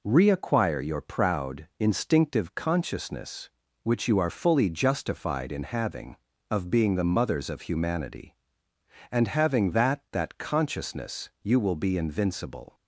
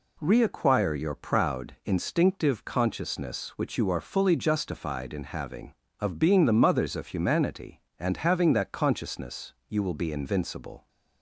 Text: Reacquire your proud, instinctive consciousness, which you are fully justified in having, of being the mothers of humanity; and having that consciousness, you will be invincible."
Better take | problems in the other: second | says "that" twice; at 10.1 s

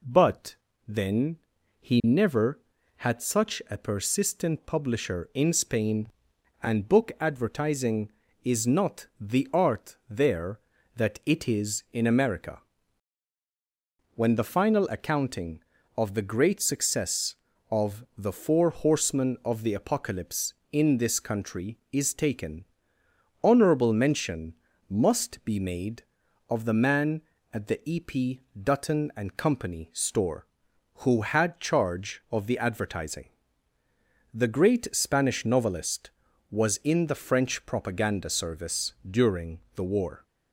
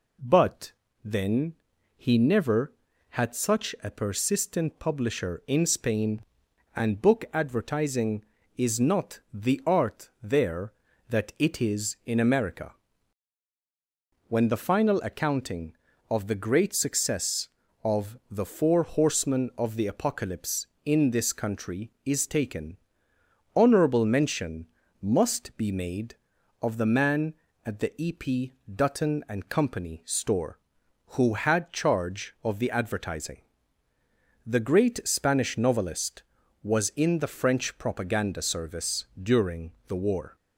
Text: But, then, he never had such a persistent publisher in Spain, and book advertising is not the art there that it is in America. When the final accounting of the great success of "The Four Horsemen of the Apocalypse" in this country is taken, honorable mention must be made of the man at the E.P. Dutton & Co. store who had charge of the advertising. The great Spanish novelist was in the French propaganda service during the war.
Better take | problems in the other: neither | pauses between "mention" and "must"; slight; the same in both // pauses between "service" and "during"; slight; the same in both // pauses between "during" and "the"; slight; the same in both

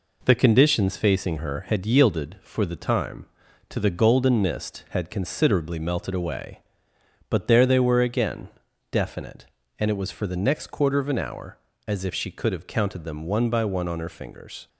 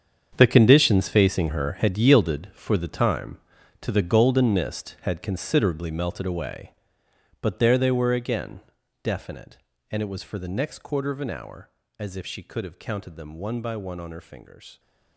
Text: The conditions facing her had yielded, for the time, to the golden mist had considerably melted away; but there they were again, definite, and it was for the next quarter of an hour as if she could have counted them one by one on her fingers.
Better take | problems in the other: first | gets quieter; strong; throughout; 13 dB

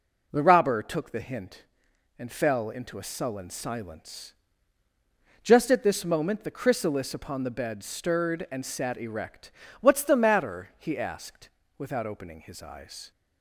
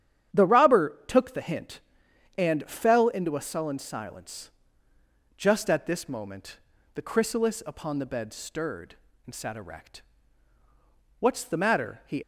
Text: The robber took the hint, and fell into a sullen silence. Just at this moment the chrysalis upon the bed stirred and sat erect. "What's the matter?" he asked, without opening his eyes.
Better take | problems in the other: first | starts louder than the rest; strong; until 1.4 s; 10 dB // pauses between "moment" and "the"; slight; at 6.5 s; 0.36 s long // stops before "asked without opening his eyes"; at 12.2 s

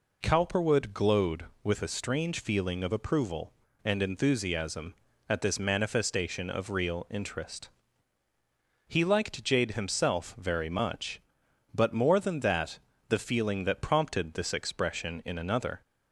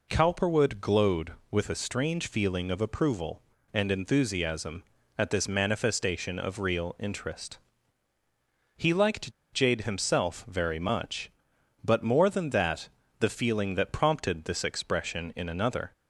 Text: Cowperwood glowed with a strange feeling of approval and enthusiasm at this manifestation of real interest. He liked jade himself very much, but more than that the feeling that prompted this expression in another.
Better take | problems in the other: first | pauses between "liked" and "jade"; slight; at 9.3 s; 0.21 s long // pauses between "that" and "the"; slight; at 12.8 s; 0.30 s long; slight in the first

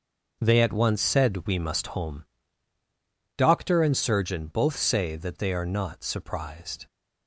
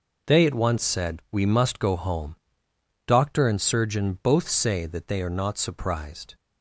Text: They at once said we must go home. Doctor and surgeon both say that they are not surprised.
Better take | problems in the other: second | skips "go"; at 1.8 s

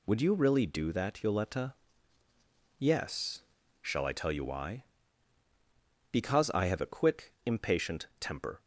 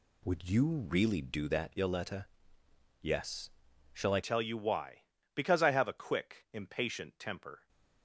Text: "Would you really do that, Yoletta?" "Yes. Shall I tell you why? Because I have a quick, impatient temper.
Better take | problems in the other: first | changes voice at "tell"; from 4.2 s on; 3.4 s long

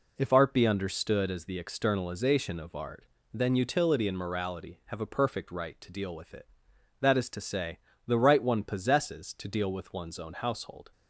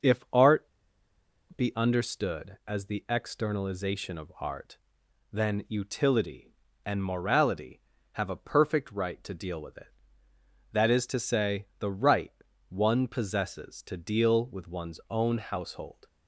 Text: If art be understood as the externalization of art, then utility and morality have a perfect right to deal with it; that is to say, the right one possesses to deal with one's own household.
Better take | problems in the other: first | pauses between "art" and "be"; noticeable; at 0.6 s; 0.94 s long // pauses between "right" and "one"; at 12.3 s; 0.40 s long

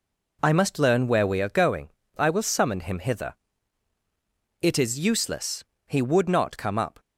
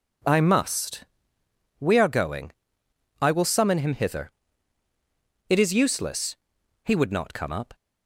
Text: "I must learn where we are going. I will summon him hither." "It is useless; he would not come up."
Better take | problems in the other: first | skips "learn where"; at 1.4 s

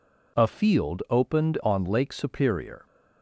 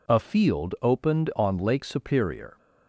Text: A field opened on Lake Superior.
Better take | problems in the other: neither | none

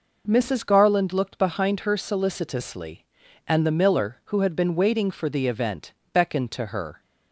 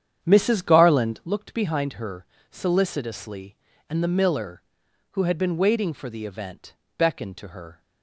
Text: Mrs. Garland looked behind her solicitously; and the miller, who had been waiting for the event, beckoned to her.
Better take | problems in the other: first | starts louder than the rest; strong; until 1.3 s; 8.5 dB // pauses between "her" and "solicitously"; slight; at 2.2 s; 0.26 s long

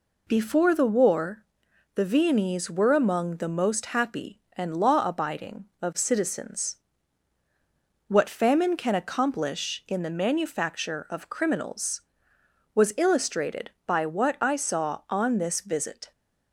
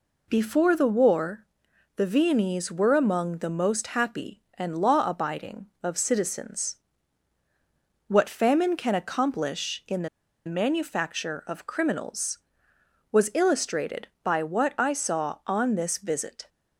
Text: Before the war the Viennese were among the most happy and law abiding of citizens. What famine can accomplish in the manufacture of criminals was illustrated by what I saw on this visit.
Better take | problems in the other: first | pauses between "war" and "the"; noticeable; at 1.4 s; 0.50 s long; noticeable in the first // pauses between "the" and "manufacture"; at 10.0 s; 0.37 s long

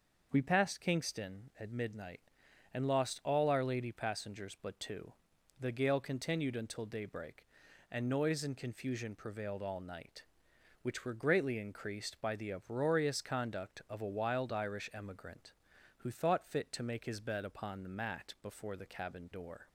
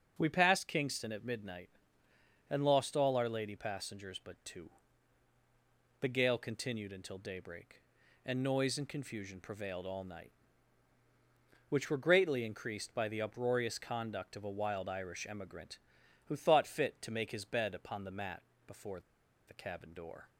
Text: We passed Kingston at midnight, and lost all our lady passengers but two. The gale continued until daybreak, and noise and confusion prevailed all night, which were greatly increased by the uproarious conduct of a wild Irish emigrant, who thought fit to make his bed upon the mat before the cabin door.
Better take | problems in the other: first | starts louder than the rest; strong; until 1.2 s; 7.5 dB; noticeable in the first // pauses between "mat" and "before"; slight; at 18.4 s; 0.24 s long // pauses between "before" and "the"; noticeable; at 18.9 s; 0.48 s long

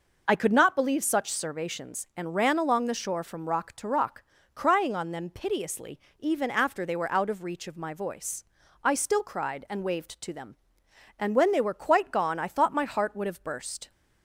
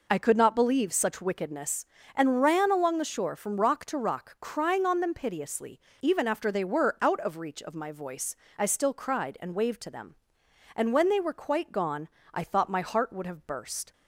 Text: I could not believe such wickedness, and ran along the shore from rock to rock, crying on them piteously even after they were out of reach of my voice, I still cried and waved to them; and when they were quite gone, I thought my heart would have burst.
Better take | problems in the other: second | says "servations" for "wickedness"; at 1.3 s // pauses between "piteously" and "even"; slight; at 5.9 s; 0.18 s long; slight in the second

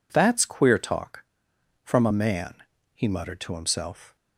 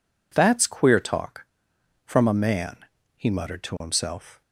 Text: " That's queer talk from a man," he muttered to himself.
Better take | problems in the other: neither | none

